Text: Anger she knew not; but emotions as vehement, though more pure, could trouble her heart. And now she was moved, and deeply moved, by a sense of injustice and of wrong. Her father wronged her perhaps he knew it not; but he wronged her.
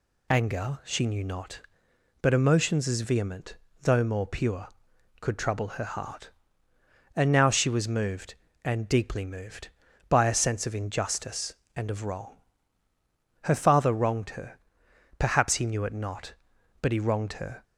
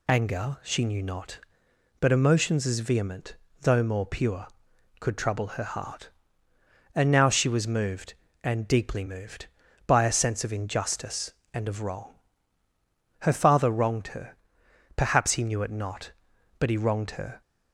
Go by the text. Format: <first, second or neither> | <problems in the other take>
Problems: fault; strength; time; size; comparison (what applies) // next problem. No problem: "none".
neither | pauses between "her" and "perhaps"; noticeable; the same in both